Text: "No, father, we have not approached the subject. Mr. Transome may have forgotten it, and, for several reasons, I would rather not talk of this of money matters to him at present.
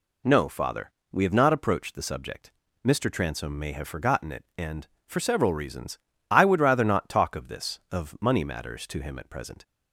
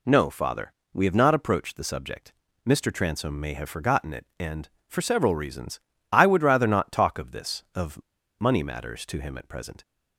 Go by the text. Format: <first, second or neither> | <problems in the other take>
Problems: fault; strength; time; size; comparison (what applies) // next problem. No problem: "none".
first | pauses between "of" and "money"; at 8.0 s; 0.39 s long